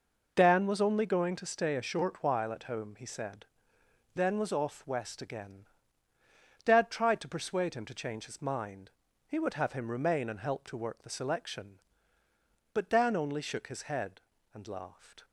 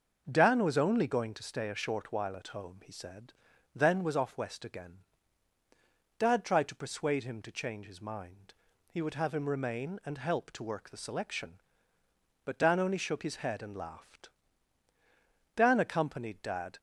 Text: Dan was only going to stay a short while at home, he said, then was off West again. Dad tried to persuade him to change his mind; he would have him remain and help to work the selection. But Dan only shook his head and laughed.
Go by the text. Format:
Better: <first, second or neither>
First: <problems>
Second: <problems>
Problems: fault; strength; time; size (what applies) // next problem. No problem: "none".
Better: first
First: none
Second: goes on to say "Dan accompanied Dad"; noticeable; from 15.5 s on; 1.2 s long